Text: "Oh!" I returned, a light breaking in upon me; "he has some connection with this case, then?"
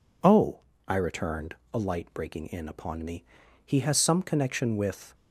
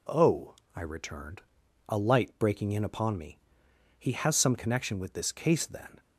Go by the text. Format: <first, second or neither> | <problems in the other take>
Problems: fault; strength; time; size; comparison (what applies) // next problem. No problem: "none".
second | stops before "this case then"; at 5.1 s